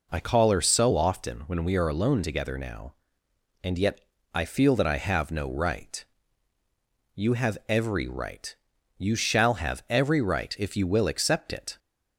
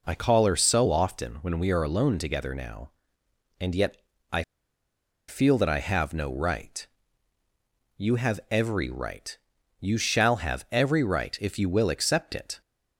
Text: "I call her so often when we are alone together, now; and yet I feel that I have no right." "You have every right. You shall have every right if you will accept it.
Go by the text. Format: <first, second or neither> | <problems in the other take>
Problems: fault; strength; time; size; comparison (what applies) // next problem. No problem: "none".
first | pauses between "yet" and "I"; slight; at 3.9 s; 0.34 s long; slight in the first // pauses between "I" and "feel"; noticeable; at 4.4 s; 0.86 s long